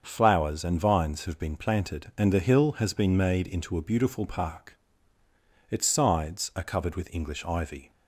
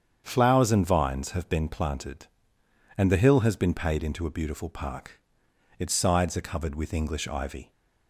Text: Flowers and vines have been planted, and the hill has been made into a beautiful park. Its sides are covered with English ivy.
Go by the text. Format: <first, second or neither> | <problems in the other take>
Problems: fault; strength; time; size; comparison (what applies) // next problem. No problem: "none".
first | starts louder than the rest; strong; until 1.2 s; 8 dB; also in the first // says "paid" for "made"; at 3.7 s